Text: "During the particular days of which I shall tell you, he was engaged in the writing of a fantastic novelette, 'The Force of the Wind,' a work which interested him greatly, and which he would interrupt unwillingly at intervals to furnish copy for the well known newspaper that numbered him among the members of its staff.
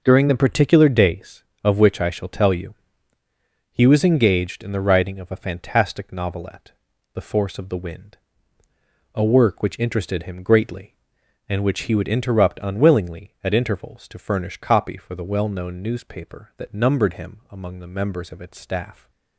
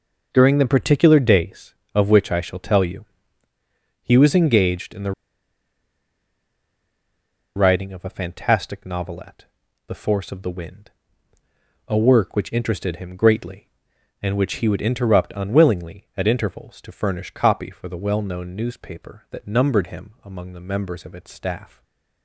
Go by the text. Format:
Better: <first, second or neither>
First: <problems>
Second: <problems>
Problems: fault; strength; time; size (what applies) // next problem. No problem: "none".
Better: first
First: none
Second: pauses between "the" and "writing"; strong; at 5.1 s; 2.4 s long // stays silent after the last word; slight; from 21.6 s on; 0.6 s long